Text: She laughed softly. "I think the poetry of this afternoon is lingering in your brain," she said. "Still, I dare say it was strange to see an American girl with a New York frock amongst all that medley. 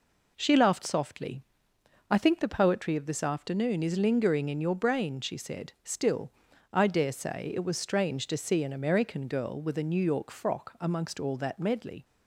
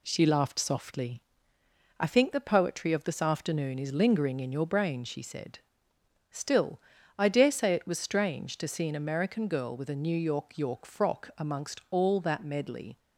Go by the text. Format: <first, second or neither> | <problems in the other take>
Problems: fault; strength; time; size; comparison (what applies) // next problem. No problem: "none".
first | says "York" twice; at 10.5 s